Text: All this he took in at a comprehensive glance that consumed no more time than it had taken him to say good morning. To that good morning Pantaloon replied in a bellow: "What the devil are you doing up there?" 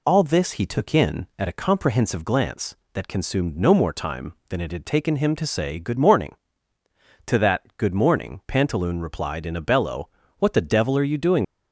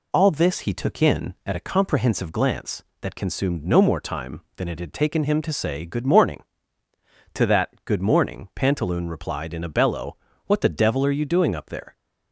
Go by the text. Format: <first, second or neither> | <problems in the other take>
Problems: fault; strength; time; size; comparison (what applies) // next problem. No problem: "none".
second | stops before "up there"; at 11.4 s